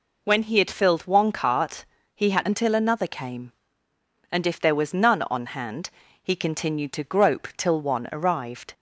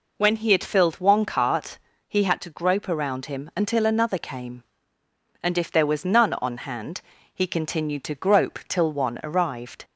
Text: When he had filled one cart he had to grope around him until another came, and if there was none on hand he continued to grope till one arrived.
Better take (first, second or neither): second